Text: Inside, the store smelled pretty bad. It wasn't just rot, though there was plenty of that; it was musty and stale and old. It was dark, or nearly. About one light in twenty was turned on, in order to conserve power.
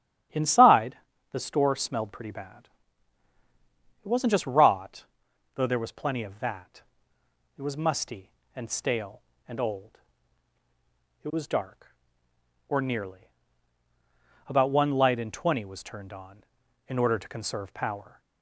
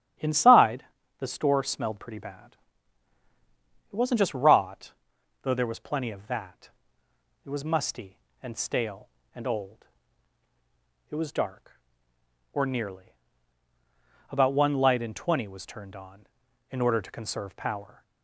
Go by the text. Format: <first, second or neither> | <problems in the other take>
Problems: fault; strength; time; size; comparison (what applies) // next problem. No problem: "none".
neither | starts louder than the rest; strong; the same in both